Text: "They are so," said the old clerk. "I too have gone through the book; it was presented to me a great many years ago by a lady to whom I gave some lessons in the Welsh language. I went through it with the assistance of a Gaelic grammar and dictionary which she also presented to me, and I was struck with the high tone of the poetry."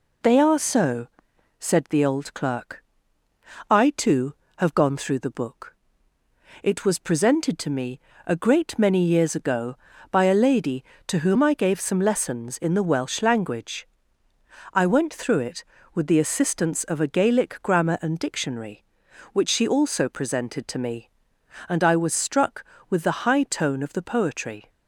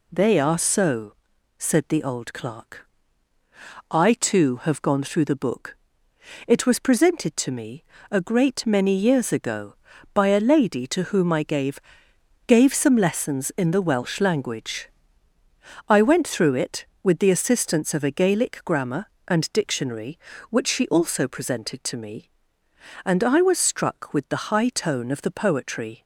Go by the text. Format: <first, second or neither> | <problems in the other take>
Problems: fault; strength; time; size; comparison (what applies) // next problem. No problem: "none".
first | pauses between "me" and "a"; slight; at 7.8 s; 0.26 s long; slight in the first // says "gave" twice; at 12.4 s